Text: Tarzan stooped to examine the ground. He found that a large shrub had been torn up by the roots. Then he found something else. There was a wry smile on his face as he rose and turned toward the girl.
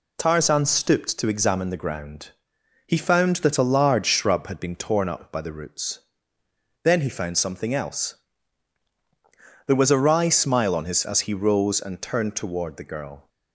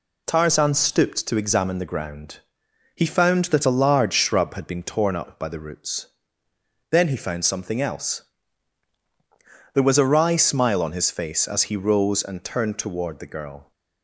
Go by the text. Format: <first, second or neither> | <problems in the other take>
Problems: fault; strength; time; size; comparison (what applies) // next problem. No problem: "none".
second | skips "face"; at 11.0 s